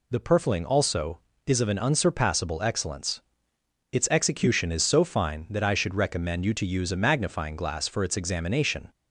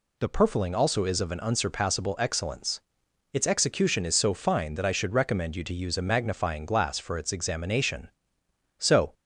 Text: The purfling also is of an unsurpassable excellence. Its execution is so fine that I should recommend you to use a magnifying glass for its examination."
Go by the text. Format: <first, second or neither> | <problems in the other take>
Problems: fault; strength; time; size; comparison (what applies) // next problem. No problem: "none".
first | goes on to say "So"; slight; from 8.7 s on; 0.34 s long